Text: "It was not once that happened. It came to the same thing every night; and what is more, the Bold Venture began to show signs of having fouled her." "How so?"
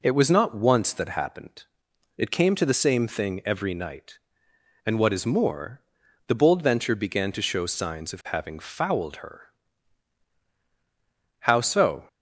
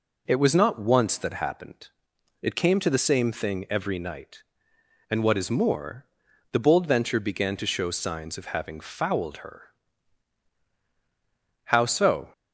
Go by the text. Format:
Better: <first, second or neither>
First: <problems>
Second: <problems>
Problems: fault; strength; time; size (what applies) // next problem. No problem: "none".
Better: neither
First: none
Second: none